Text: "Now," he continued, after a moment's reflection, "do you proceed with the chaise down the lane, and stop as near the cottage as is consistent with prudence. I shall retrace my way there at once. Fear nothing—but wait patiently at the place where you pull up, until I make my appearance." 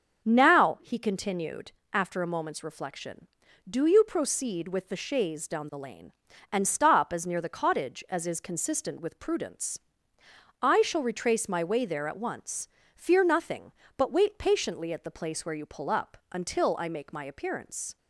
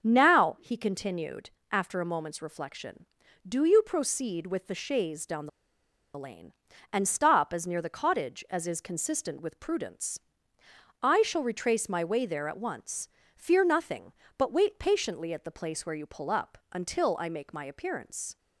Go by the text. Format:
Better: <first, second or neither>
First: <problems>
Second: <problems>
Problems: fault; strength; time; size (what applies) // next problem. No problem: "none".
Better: first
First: starts louder than the rest; until 1.2 s; 6.5 dB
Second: starts louder than the rest; until 1.0 s; 6.5 dB // pauses between "the" and "lane"; noticeable; at 5.4 s; 0.67 s long